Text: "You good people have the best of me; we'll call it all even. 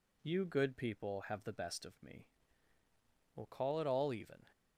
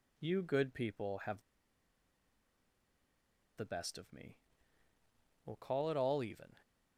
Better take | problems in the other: first | pauses between "have" and "the"; strong; at 1.4 s; 2.1 s long

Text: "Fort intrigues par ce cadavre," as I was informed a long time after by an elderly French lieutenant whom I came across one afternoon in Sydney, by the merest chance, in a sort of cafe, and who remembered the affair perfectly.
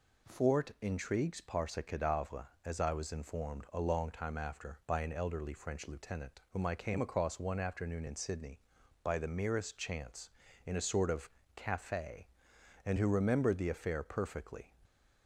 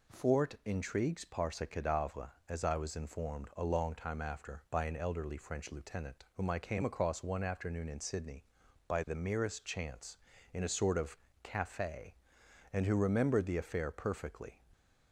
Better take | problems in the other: neither | pauses between "of" and "cafe"; slight; the same in both

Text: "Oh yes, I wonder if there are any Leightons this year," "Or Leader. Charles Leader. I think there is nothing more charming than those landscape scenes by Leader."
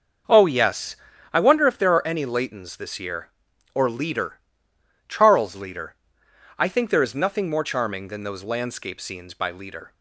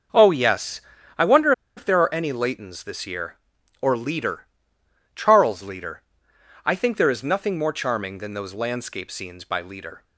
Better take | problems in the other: first | starts louder than the rest; until 1.5 s; 6.5 dB; also in the first // pauses between "wonder" and "if"; slight; at 1.5 s; 0.25 s long

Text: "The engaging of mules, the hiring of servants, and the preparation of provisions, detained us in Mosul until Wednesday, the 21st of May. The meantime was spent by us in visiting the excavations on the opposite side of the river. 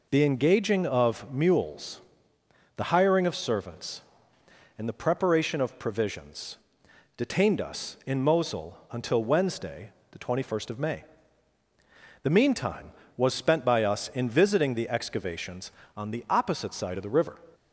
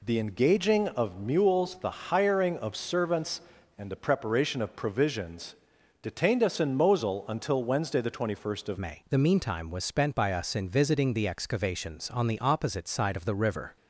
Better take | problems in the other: first | changes voice at "May"; from 8.7 s on; 5.0 s long

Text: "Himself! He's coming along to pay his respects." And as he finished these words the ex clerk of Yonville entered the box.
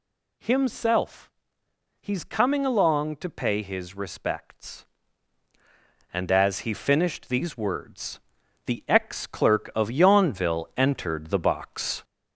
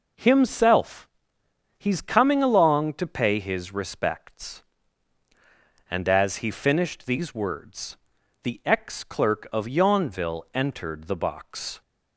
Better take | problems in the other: second | gets louder; throughout; 3.5 dB // pauses between "words" and "the"; noticeable; at 8.1 s; 0.46 s long; noticeable in the second

